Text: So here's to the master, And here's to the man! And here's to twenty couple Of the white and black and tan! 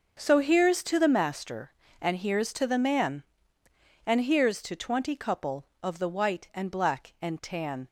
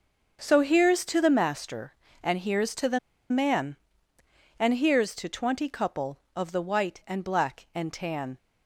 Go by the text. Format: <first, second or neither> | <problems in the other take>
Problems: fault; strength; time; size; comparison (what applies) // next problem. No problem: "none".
first | starts louder than the rest; until 1.4 s; 6 dB; also in the first // pauses between "the" and "man"; slight; at 2.9 s; 0.32 s long